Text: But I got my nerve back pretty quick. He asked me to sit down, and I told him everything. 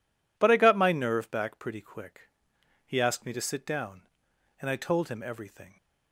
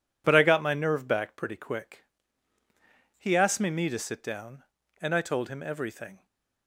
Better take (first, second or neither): first